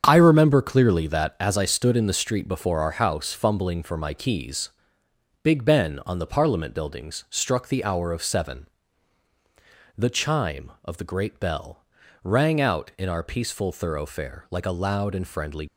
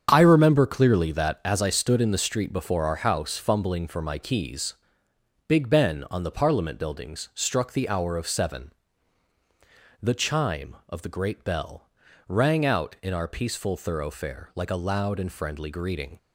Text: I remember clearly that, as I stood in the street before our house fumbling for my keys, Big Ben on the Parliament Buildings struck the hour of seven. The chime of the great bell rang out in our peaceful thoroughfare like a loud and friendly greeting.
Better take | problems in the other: second | starts louder than the rest; strong; until 1.0 s; 7.5 dB; strong in the second // pauses between "bell" and "rang"; at 11.8 s; 0.38 s long; also in the second // stops before "greeting"; at 15.6 s

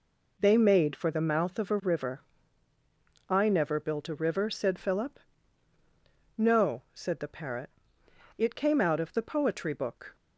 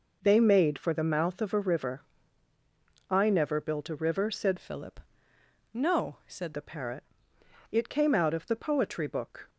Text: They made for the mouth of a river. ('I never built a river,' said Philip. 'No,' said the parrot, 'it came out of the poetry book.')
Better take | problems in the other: first | changes voice from "Philip" to "said"; from 4.5 to 6.5 s; 2.0 s long

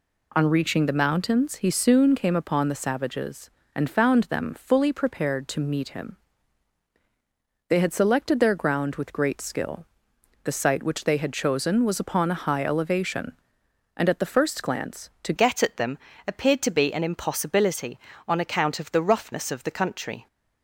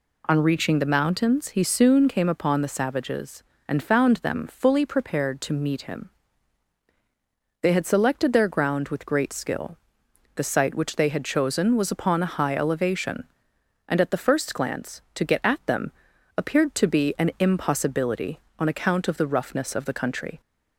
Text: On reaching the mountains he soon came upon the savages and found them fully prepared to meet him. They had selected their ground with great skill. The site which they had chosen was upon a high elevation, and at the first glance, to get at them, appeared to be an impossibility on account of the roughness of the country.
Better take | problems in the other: second | changes voice at "get"; from 15.3 s on; 4.9 s long

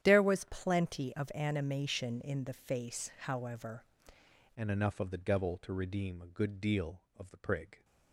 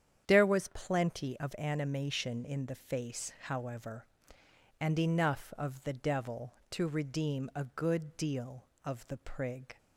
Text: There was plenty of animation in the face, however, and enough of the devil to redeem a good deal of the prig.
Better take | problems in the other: second | starts louder than the rest; strong; until 1.0 s; 10 dB; strong in the second // changes voice at "and"; from 4.5 s on; 3.3 s long

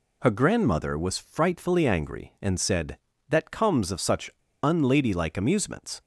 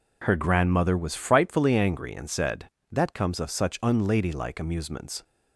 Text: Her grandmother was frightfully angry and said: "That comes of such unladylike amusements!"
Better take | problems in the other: second | pauses between "such" and "unladylike"; slight; at 4.3 s; 0.31 s long

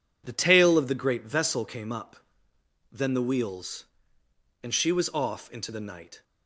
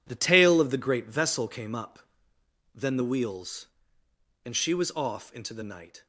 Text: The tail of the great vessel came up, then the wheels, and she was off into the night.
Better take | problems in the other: first | gets quieter; strong; throughout; 11.5 dB

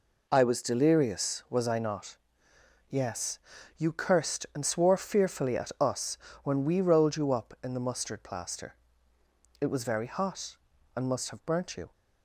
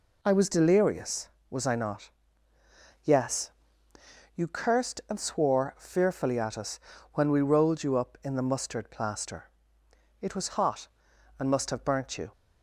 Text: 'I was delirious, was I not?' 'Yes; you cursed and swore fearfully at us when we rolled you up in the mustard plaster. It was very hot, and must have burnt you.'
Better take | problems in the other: first | pauses between "us" and "when"; slight; at 6.7 s; 0.34 s long; slight in the first // skips "very"; at 10.4 s

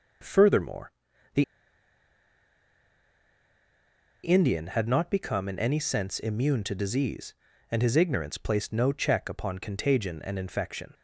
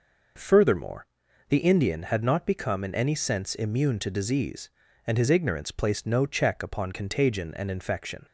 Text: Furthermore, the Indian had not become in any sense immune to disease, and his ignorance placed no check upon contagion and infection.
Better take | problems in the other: second | pauses between "the" and "Indian"; strong; at 1.4 s; 2.8 s long

